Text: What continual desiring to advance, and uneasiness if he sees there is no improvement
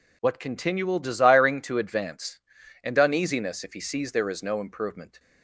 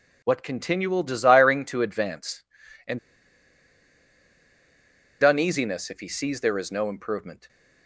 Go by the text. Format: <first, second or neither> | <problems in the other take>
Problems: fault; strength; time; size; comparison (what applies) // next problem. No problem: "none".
first | pauses between "and" and "uneasiness"; strong; at 2.9 s; 2.2 s long